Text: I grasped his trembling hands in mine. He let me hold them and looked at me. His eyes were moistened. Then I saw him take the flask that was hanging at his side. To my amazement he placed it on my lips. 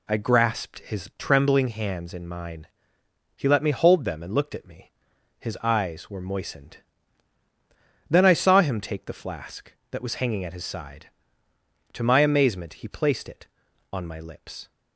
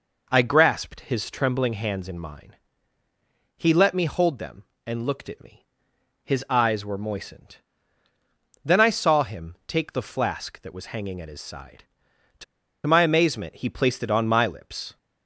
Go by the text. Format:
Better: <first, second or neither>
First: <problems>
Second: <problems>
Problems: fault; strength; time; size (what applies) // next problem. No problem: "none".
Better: first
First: none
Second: pauses between "To" and "my"; at 12.4 s; 0.42 s long